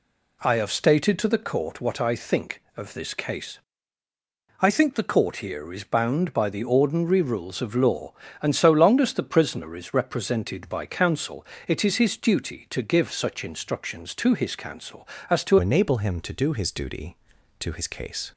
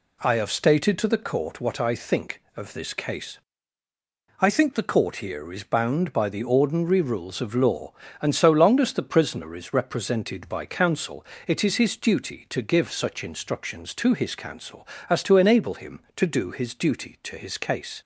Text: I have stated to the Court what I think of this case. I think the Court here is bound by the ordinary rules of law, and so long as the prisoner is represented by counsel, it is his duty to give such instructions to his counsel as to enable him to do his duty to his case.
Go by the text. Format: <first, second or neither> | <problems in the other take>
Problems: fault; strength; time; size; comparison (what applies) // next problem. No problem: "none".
second | changes voice at "enable"; from 15.5 s on; 2.8 s long